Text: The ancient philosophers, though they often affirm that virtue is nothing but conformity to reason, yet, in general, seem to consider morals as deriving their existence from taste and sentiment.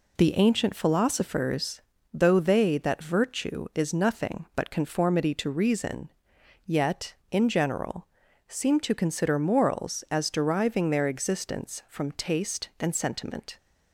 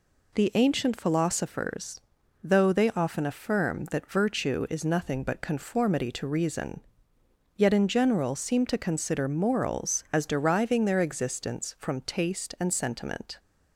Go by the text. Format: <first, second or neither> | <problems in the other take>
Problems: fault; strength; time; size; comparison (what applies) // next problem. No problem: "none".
second | skips "often affirm"; at 2.7 s